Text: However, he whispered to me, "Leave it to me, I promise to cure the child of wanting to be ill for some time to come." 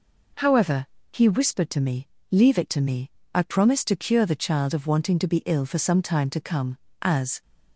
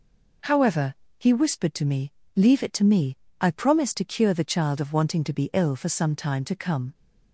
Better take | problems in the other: second | goes on to say "As"; slight; from 7.0 s on; 0.40 s long

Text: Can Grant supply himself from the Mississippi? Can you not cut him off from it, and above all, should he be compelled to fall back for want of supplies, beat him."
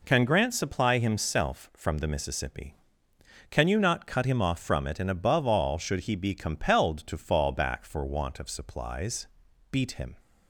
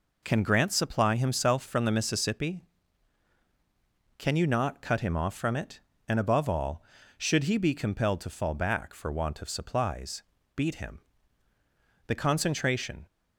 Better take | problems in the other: first | goes on to say "The concentration"; noticeable; from 12.0 s on; 1.0 s long

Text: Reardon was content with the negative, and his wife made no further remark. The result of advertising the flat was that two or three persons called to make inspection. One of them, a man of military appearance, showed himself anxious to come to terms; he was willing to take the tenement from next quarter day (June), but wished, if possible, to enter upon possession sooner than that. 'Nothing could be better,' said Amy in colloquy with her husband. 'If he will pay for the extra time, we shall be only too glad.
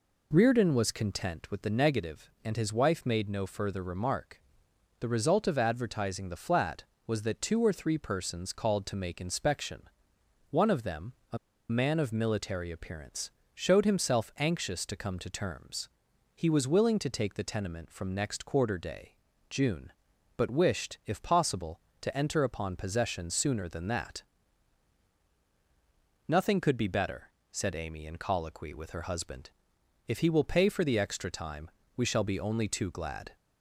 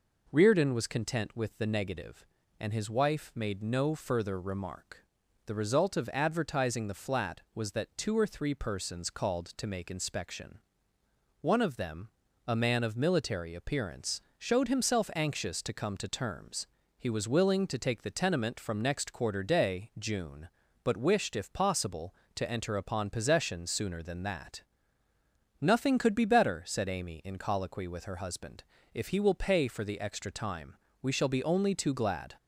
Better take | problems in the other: second | pauses between "a" and "man"; slight; at 11.3 s; 0.32 s long

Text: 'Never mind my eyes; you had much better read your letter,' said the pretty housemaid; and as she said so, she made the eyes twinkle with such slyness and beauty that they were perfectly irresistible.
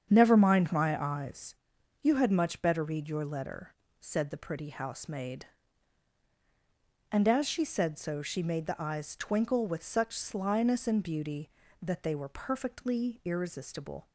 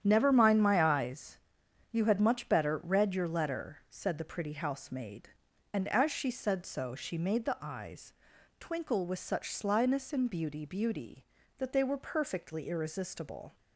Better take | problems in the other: first | starts louder than the rest; strong; until 1.0 s; 9.5 dB; strong in the first // pauses between "eyes" and "twinkle"; at 8.1 s; 0.44 s long // says "beauty" twice; at 10.6 s

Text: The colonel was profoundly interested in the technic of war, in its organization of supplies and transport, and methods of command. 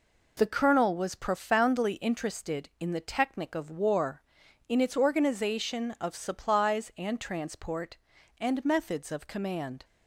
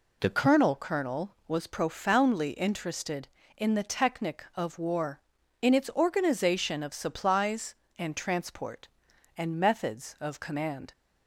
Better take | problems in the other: first | says "colonel" twice; at 0.7 s

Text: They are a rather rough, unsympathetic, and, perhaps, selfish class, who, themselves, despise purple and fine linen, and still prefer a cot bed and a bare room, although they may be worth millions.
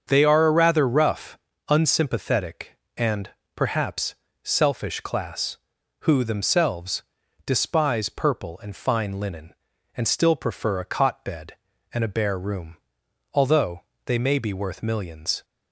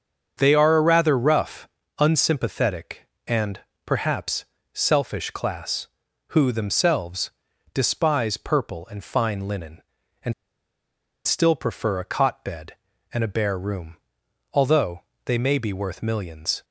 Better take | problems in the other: first | starts louder than the rest; until 1.3 s; 7 dB; also in the first // pauses between "and" and "still"; noticeable; at 10.3 s; 0.94 s long // pauses between "although" and "they"; slight; at 15.0 s; 0.24 s long; slight in the first

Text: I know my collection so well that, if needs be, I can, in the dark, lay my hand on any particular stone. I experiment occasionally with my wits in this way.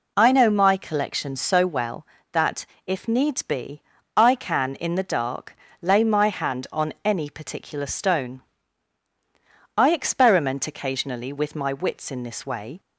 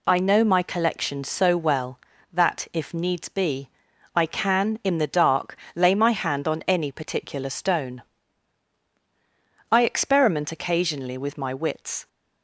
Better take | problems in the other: first | stops before "in this way"; at 12.0 s

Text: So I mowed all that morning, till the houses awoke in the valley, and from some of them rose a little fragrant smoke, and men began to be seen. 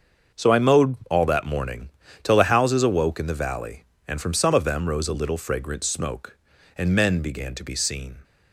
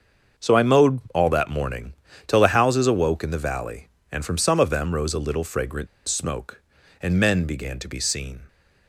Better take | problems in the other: first | starts louder than the rest; until 1.5 s; 6.5 dB; also in the first // pauses between "fragrant" and "smoke"; slight; at 5.8 s; 0.19 s long

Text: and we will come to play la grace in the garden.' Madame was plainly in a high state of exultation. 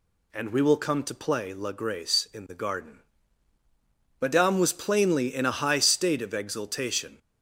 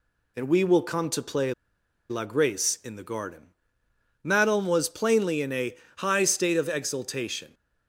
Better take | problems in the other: first | pauses between "play" and "la"; noticeable; at 1.5 s; 0.57 s long // pauses between "a" and "high"; slight; at 5.7 s; 0.24 s long

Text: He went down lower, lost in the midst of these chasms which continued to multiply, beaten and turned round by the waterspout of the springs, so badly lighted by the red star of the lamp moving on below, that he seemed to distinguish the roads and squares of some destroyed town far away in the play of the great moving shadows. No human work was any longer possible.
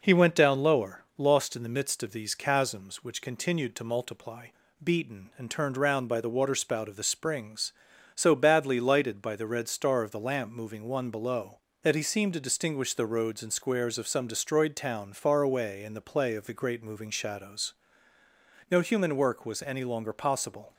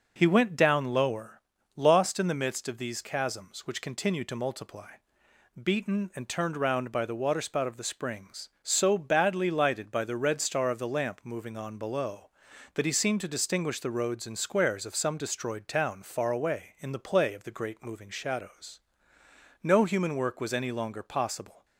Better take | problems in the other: second | says "one" for "on"; at 10.8 s

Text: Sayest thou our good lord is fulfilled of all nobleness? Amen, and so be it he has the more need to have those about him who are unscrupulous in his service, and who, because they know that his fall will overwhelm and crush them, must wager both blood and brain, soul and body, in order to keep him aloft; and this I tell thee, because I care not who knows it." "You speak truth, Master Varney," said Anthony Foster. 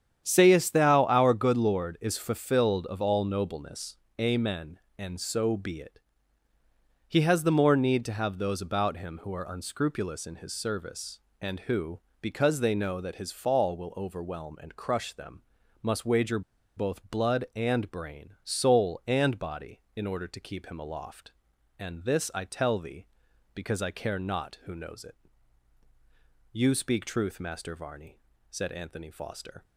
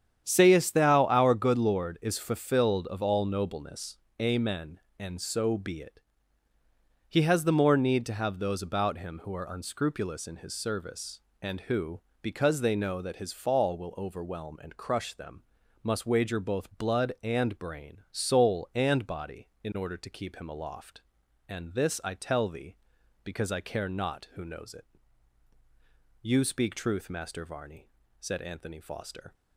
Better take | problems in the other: second | starts louder than the rest; strong; until 1.2 s; 9 dB; strong in the second // pauses between "it" and "he"; at 5.9 s; 1.0 s long; also in the second // pauses between "wager" and "both"; slight; at 16.4 s; 0.36 s long

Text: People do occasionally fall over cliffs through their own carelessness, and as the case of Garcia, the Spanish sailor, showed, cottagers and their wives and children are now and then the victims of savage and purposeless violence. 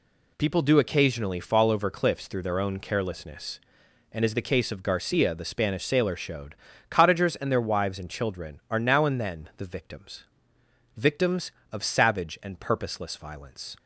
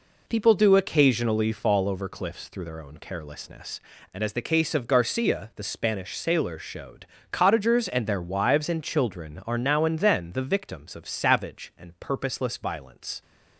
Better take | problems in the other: second | says "victims" twice; at 10.9 s

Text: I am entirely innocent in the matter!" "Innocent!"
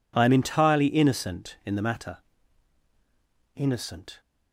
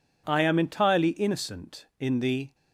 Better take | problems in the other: first | stops before "matter Innocent"; at 2.5 s

